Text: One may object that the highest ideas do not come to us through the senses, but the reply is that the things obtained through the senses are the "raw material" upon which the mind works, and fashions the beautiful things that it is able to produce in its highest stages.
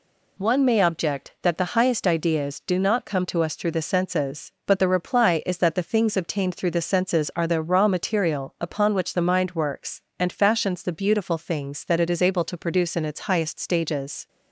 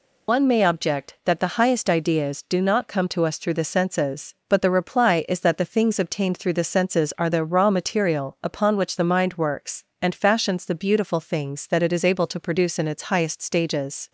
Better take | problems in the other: first | loses the start of "One"; at 0.2 s; 80 ms

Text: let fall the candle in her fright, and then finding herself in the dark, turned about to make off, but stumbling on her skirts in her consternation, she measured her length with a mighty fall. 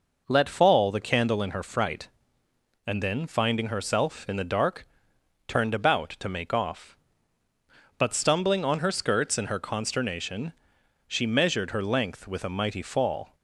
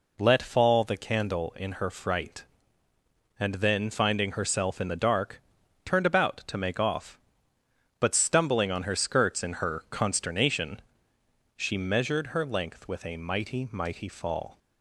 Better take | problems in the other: first | says "mighty" twice; at 13.7 s

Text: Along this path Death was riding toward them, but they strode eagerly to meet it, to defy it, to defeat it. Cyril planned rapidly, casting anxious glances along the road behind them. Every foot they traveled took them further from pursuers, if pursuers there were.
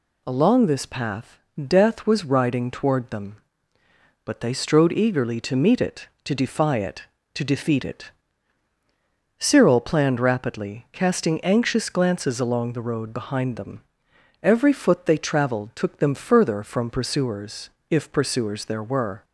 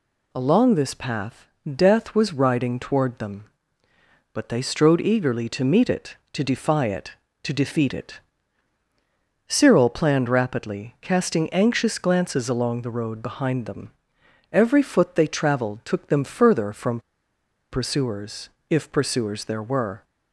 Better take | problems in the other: first | pauses between "path" and "Death"; slight; at 1.4 s; 0.28 s long; slight in the first // pauses between "from" and "pursuers"; noticeable; at 17.0 s; 0.70 s long

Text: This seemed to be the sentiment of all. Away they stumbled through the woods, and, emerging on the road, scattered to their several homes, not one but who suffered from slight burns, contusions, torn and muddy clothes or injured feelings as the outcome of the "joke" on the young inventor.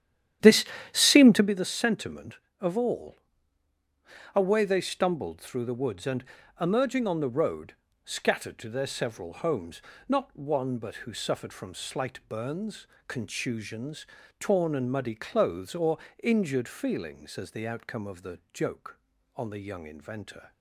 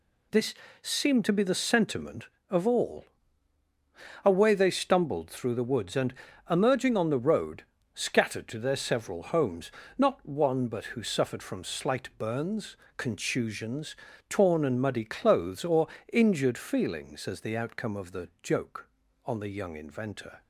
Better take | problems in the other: second | starts louder than the rest; strong; until 1.5 s; 11 dB // pauses between "This" and "seemed"; slight; at 0.6 s; 0.28 s long; slight in the second // pauses between "or" and "injured"; slight; at 15.9 s; 0.24 s long; slight in the second // pauses between "the" and "joke"; slight; at 18.3 s; 0.16 s long; slight in the second

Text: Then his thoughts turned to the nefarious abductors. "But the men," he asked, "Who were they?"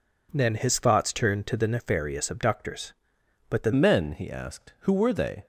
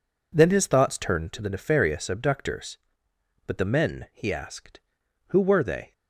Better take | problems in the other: second | changes voice at "men"; from 3.7 s on; 1.7 s long

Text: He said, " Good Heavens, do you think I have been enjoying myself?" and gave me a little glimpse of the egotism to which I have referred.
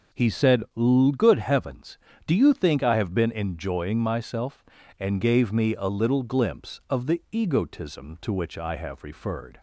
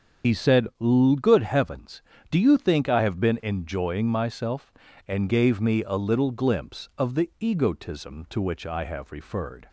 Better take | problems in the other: first | loses the start of "He"; at 0.2 s; 70 ms

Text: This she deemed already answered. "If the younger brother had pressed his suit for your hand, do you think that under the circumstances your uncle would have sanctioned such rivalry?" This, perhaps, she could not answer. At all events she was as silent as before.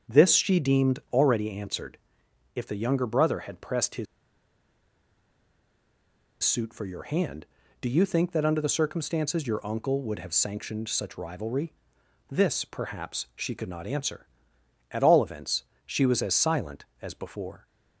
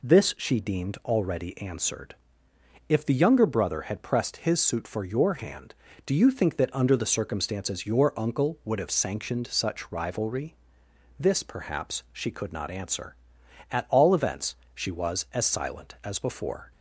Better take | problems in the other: second | starts louder than the rest; strong; until 1.2 s; 7.5 dB // pauses between "his" and "suit"; strong; at 4.0 s; 2.3 s long // pauses between "events" and "she"; slight; at 15.6 s; 0.20 s long; slight in the second

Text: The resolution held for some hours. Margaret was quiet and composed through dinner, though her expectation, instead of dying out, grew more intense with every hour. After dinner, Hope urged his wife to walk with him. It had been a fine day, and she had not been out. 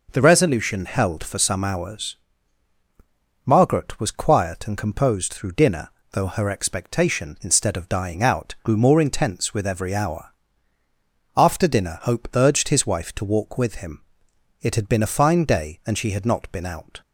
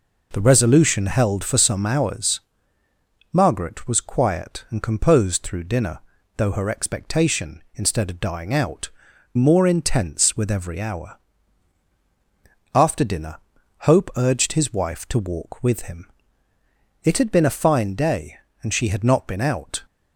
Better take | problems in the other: first | skips "grew"; at 9.1 s

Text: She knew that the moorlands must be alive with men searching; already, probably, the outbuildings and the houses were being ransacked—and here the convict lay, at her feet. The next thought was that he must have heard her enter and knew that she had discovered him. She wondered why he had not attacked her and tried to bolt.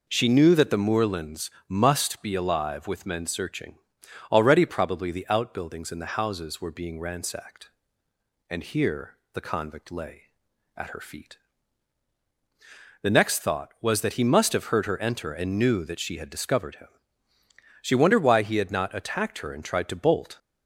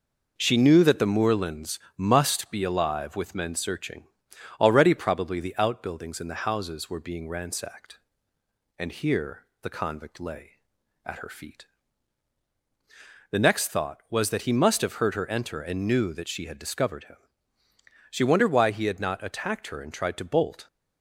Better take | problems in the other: first | gets quieter; slight; throughout; 3 dB // pauses between "moorlands" and "must"; slight; at 1.7 s; 0.18 s long; slight in the first // pauses between "here" and "the"; slight; at 9.4 s; 0.18 s long; slight in the first

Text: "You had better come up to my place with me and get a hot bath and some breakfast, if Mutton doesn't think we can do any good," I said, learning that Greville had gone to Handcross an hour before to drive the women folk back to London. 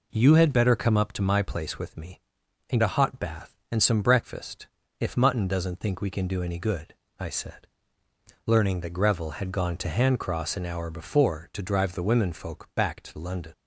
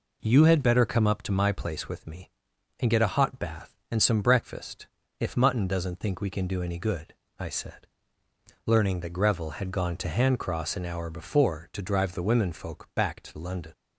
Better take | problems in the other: second | skips "get"; at 2.8 s

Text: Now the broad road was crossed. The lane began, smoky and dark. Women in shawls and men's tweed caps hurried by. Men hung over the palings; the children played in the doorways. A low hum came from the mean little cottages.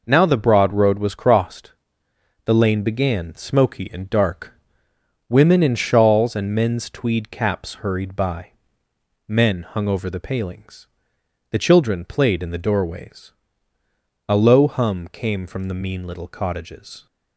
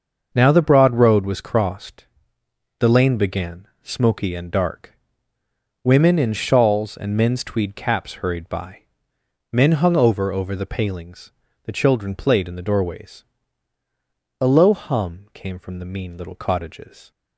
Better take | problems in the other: first | starts louder than the rest; until 1.3 s; 6 dB // says "over" twice; at 10.3 s

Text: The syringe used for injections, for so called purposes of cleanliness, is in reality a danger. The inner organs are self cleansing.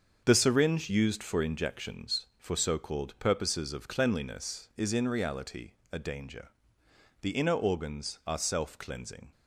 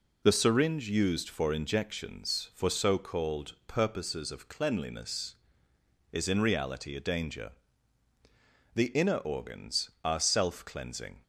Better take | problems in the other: second | gets quieter; strong; throughout; 7.5 dB // pauses between "reality" and "a"; slight; at 5.7 s; 0.20 s long

